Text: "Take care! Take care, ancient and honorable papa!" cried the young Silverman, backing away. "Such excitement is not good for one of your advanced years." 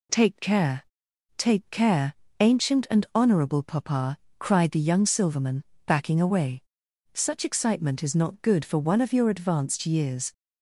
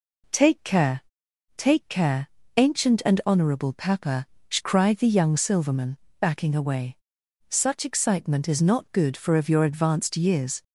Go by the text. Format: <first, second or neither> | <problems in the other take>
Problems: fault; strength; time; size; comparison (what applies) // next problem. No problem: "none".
first | skips "one"; at 9.3 s